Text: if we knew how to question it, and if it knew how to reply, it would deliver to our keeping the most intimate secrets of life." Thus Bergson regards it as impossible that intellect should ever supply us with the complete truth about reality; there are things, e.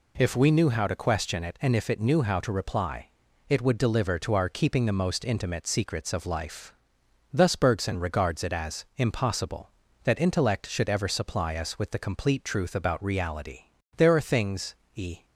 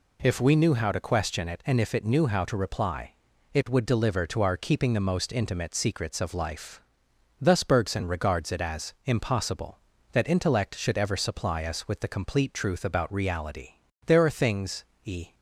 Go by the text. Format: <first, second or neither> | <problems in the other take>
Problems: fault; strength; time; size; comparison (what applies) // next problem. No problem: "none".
neither | none